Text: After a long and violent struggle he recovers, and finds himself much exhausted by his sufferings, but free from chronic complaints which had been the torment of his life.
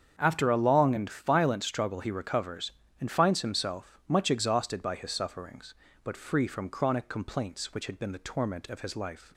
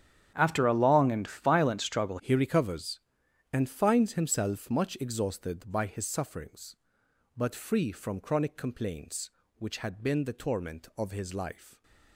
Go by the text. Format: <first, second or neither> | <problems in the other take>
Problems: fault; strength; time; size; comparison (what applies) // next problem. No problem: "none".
first | starts louder than the rest; strong; until 1.3 s; 9 dB; strong in the first // changes voice at "he"; from 2.1 s on; 9.7 s long